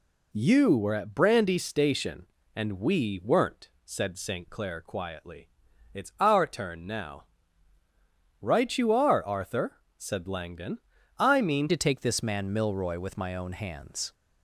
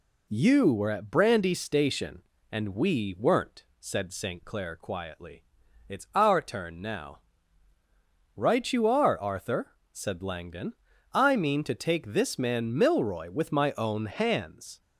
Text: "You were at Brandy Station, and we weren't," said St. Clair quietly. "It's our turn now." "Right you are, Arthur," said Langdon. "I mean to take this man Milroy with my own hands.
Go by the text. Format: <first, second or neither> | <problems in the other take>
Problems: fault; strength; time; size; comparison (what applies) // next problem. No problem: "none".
second | changes voice at "to"; from 11.6 s on; 2.5 s long